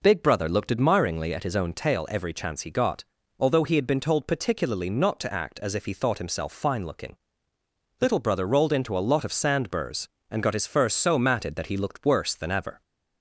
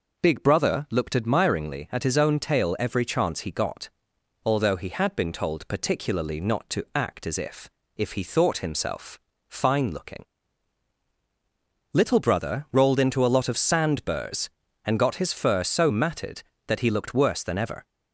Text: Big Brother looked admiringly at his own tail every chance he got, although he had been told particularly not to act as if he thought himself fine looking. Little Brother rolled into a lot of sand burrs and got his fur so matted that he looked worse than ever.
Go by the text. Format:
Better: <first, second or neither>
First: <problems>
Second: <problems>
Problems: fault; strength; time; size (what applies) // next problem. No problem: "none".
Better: first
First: none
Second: says "if" twice; at 7.9 s // pauses between "himself" and "fine"; slight; at 9.1 s; 0.28 s long